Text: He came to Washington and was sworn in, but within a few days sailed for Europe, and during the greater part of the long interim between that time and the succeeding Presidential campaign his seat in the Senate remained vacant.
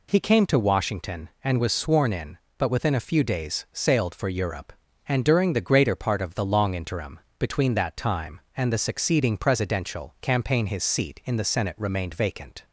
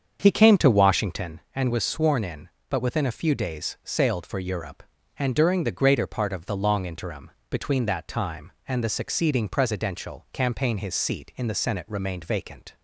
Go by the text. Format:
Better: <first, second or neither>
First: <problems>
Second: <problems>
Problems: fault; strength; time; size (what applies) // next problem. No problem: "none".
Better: first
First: pauses between "interim" and "between"; slight; at 7.1 s; 0.18 s long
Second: starts louder than the rest; strong; until 1.3 s; 7 dB // pauses between "interim" and "between"; slight; at 7.2 s; 0.18 s long